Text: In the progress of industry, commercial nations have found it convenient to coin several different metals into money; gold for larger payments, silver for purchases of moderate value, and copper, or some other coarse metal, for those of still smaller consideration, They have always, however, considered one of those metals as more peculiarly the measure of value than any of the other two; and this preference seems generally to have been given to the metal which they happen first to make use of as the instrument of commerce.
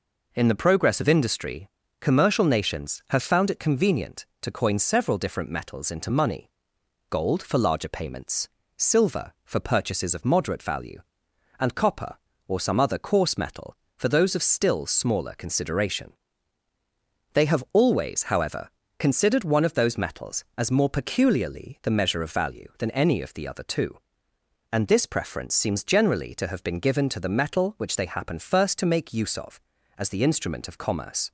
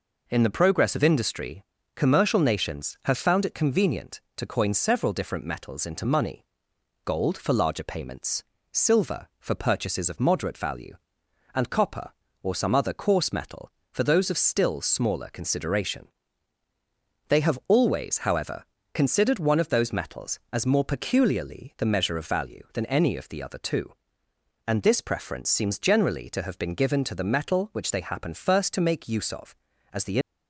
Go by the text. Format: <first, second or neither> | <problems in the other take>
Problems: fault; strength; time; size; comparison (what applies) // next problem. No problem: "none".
first | stops before "instrument of commerce"; at 30.2 s